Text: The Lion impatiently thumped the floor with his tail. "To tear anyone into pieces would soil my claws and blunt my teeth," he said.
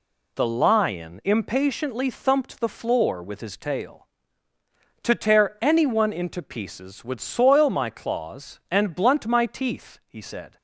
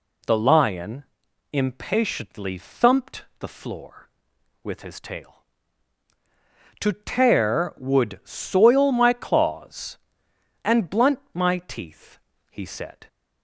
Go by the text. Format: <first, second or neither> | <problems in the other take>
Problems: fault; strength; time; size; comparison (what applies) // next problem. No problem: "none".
first | pauses between "Lion" and "impatiently"; noticeable; at 1.0 s; 0.48 s long // skips "anyone into pieces"; at 7.7 s